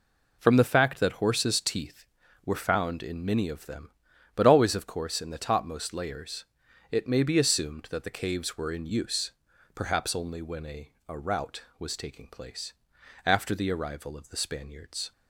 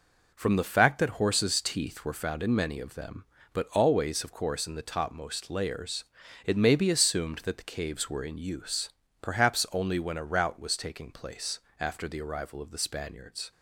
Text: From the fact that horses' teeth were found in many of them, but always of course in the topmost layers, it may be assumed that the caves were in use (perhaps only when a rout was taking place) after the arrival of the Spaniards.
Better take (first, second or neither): second